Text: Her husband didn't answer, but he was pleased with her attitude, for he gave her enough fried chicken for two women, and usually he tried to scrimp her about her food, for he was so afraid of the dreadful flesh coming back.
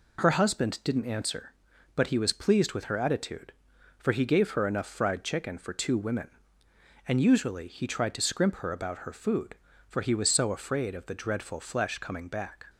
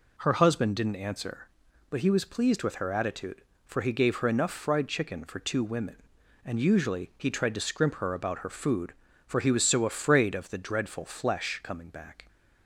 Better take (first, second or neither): neither